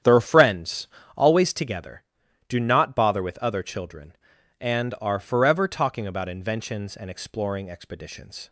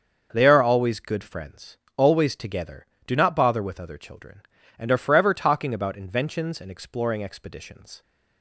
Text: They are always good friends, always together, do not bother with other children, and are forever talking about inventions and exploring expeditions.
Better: second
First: starts louder than the rest; strong; until 1.3 s; 9.5 dB // skips "always good"; at 0.2 s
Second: starts louder than the rest; until 1.3 s; 6.5 dB

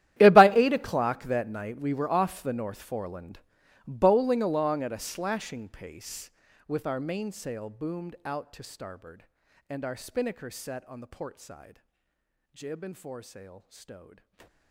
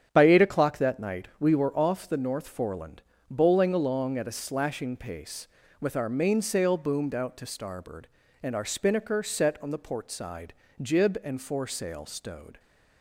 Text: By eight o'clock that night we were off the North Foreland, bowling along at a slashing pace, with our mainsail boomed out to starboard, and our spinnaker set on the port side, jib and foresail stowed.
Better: second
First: gets quieter; strong; throughout; 20 dB // starts louder than the rest; strong; until 1.2 s; 12.5 dB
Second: starts louder than the rest; strong; until 1.1 s; 8.5 dB

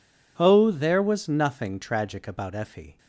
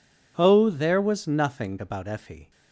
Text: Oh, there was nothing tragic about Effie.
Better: first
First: none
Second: skips "tragic"; at 1.7 s

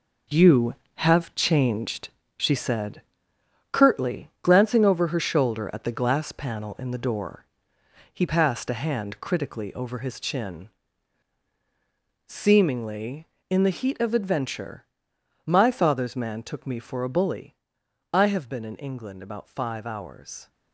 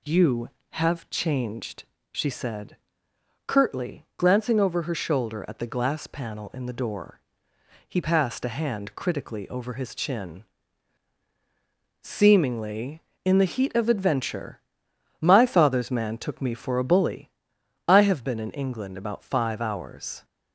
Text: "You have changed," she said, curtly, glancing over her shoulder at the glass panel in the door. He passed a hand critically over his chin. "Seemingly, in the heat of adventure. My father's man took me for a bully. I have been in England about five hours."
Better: second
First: gets quieter; strong; throughout; 8 dB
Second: none

